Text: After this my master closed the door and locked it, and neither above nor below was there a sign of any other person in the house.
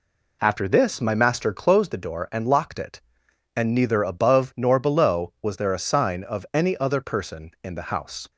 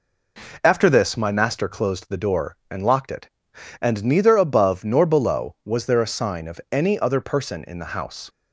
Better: neither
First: none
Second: none

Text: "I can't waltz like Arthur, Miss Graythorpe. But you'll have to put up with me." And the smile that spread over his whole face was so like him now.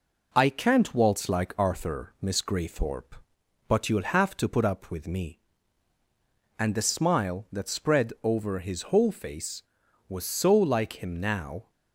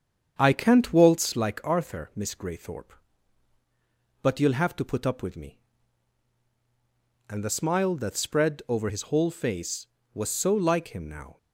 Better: first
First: none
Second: starts louder than the rest; strong; until 1.3 s; 7.5 dB

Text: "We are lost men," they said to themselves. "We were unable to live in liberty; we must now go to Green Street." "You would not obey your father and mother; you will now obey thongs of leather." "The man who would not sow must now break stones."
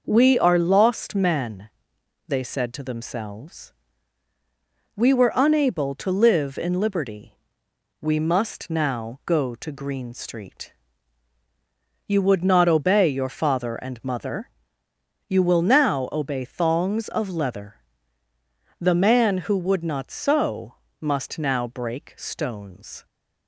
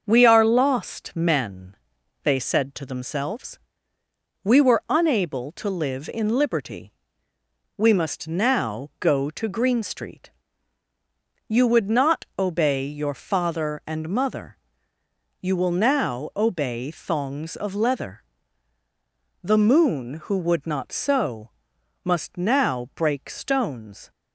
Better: first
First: pauses between "sow" and "must"; slight; at 20.7 s; 0.24 s long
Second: starts louder than the rest; until 1.0 s; 6.5 dB // says "moon" for "man"; at 19.5 s // pauses between "sow" and "must"; noticeable; at 21.5 s; 0.54 s long

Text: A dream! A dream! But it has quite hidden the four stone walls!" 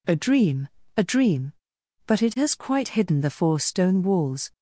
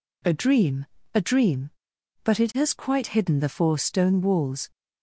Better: neither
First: none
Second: none

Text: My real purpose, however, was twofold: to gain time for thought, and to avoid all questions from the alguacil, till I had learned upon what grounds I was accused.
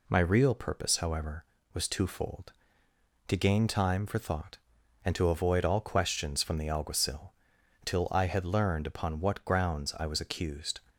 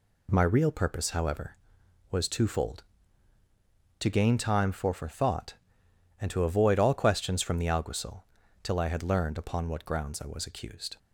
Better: first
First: none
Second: says "for" twice; at 4.9 s

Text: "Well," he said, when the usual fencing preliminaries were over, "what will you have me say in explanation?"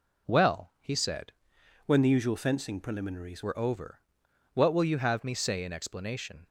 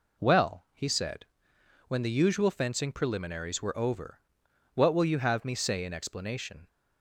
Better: second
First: changes voice from "when" to "preliminaries"; from 1.8 to 3.4 s; 1.6 s long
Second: none

